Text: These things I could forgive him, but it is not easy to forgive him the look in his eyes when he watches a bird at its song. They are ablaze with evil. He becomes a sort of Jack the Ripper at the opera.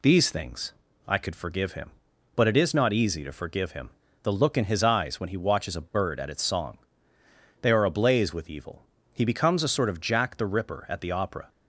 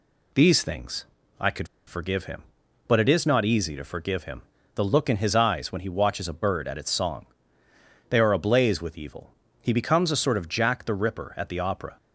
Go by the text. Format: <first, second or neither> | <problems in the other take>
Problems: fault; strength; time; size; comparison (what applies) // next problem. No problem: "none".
first | pauses between "things" and "I"; slight; at 1.0 s; 0.36 s long; slight in the first // pauses between "could" and "forgive"; slight; at 1.6 s; 0.20 s long // pauses between "him" and "the"; slight; at 4.4 s; 0.34 s long; slight in the first